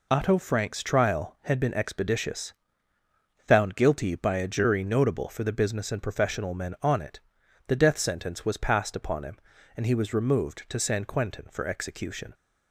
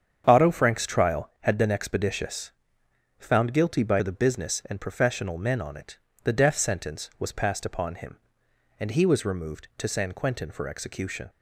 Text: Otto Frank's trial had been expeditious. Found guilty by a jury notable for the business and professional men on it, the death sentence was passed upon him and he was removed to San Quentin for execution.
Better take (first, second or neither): first